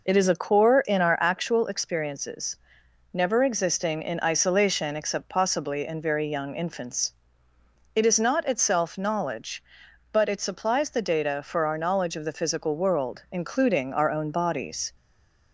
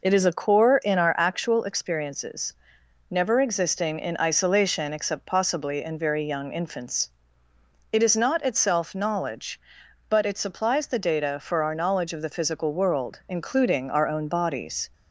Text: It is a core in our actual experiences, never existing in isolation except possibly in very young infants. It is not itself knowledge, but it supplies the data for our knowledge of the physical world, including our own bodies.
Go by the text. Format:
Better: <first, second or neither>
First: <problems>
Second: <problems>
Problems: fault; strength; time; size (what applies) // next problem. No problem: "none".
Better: second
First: stays silent after the last word; slight; from 14.9 s on; 0.6 s long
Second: none